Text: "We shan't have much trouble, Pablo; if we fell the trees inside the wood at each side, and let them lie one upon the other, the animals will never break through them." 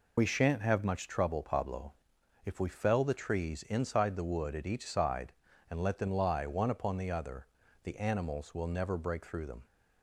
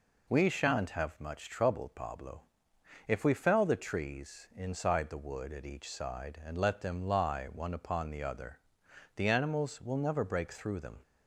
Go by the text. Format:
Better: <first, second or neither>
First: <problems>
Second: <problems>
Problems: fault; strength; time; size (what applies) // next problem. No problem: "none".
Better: second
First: loses the start of "We"; at 0.1 s; 55 ms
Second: none